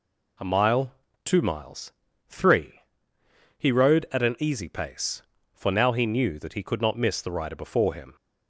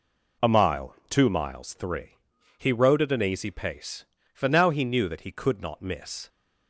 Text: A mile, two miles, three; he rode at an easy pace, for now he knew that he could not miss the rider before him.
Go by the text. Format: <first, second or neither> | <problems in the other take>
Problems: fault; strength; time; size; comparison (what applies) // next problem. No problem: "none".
first | stops before "the rider before him"; at 6.2 s